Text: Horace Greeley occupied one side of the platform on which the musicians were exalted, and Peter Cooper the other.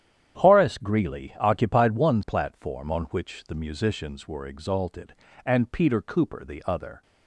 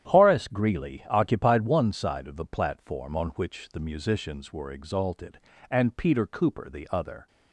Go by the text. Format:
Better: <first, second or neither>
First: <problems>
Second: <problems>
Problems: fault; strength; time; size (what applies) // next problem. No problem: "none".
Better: second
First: starts louder than the rest; strong; until 1.4 s; 10 dB // skips "side of the"; at 2.2 s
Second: starts louder than the rest; strong; until 1.1 s; 10 dB